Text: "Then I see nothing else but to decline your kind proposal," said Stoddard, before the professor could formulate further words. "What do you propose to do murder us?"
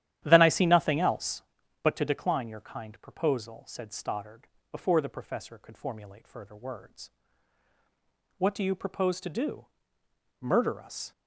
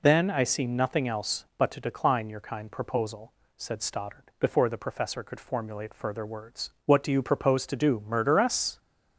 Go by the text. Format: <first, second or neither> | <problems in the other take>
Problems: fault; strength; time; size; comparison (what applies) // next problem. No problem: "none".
second | starts louder than the rest; strong; until 1.4 s; 11.5 dB // pauses between "do" and "murder"; noticeable; at 9.6 s; 0.72 s long